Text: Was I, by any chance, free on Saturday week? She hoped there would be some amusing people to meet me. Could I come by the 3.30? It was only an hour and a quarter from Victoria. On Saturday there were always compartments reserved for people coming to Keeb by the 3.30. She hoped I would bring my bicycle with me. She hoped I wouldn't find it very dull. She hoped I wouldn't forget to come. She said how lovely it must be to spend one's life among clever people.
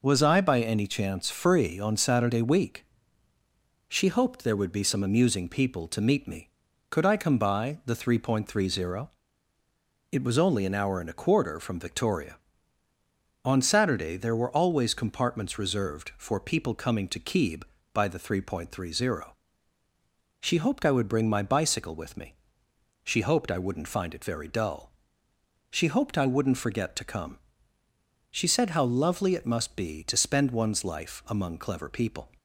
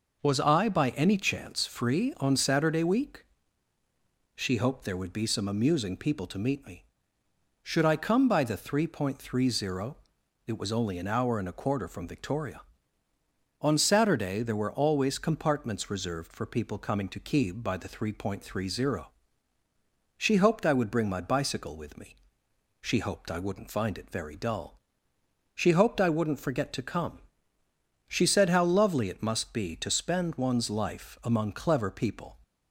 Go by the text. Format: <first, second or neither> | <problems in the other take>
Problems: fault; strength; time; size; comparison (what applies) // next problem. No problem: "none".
first | says "Should" for "Could"; at 7.6 s